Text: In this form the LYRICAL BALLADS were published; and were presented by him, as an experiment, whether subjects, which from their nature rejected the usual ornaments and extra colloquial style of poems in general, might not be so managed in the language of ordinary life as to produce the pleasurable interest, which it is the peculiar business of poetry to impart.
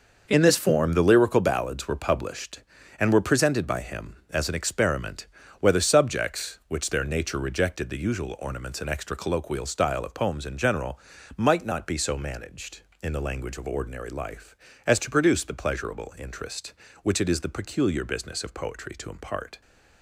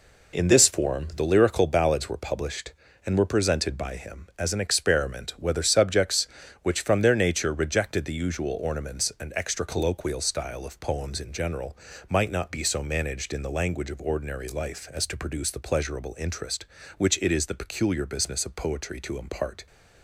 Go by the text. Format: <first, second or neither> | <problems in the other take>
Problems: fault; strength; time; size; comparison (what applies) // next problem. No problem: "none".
second | skips "from"; at 6.9 s